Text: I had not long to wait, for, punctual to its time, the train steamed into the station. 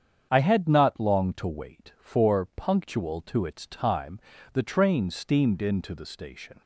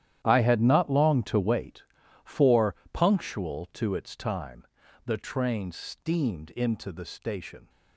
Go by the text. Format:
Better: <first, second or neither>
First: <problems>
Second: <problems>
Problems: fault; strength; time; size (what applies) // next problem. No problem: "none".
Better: first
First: starts louder than the rest; strong; until 1.3 s; 8 dB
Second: gets quieter; strong; throughout; 16 dB // starts louder than the rest; strong; until 1.2 s; 11.5 dB